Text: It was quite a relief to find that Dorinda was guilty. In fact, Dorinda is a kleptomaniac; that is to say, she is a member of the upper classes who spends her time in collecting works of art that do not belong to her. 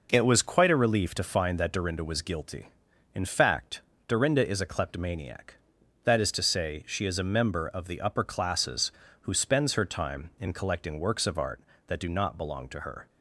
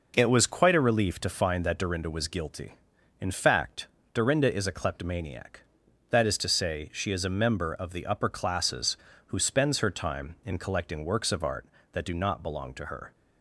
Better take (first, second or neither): neither